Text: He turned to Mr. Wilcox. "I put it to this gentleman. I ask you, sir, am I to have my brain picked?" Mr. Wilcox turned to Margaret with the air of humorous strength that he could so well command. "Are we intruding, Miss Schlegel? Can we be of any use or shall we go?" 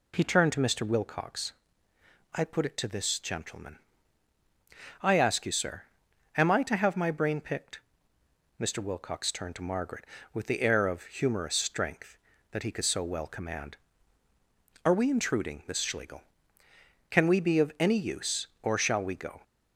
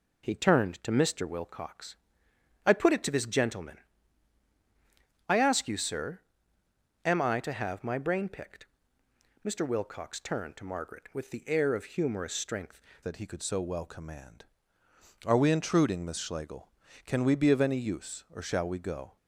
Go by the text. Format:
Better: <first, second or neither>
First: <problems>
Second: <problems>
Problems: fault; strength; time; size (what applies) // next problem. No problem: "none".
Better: first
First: none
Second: changes voice at "that"; from 13.0 s on; 6.1 s long